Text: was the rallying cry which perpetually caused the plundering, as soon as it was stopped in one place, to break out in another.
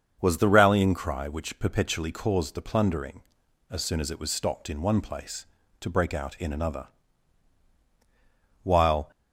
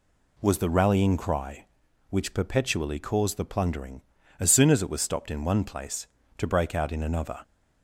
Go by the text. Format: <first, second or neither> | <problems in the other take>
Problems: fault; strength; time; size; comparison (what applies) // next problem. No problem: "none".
second | starts louder than the rest; until 1.2 s; 6.5 dB // goes on to say "While"; slight; from 8.6 s on; 0.48 s long